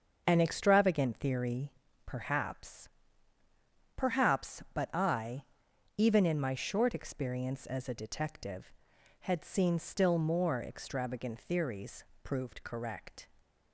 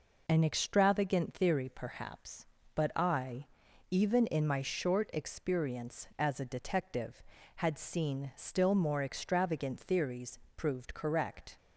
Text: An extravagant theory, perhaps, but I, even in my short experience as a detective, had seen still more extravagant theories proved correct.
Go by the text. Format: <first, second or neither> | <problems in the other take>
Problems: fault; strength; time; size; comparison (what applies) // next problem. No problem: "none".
second | starts louder than the rest; until 1.2 s; 6.5 dB // says "perhaps" twice; at 3.9 s // pauses between "theories" and "proved"; slight; at 12.0 s; 0.20 s long; slight in the second